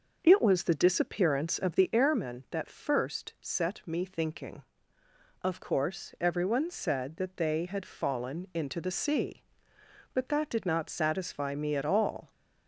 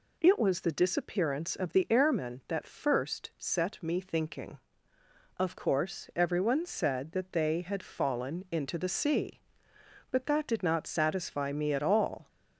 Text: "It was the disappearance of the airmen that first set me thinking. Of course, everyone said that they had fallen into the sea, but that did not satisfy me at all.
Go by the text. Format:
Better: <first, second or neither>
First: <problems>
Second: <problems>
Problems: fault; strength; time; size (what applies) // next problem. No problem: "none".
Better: second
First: starts louder than the rest; noticeable; until 1.9 s; 6 dB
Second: none